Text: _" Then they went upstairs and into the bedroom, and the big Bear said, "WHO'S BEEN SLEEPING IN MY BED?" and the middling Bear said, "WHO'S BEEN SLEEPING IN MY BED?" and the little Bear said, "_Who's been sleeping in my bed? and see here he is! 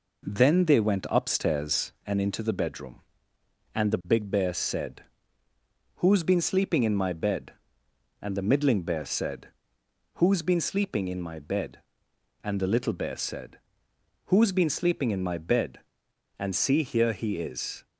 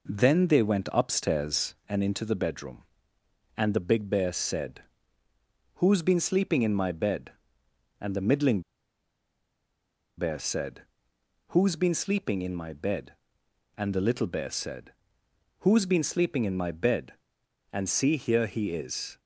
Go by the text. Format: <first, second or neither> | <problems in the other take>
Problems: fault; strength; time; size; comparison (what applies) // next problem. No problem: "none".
first | pauses between "middling" and "Bear"; strong; at 8.6 s; 1.5 s long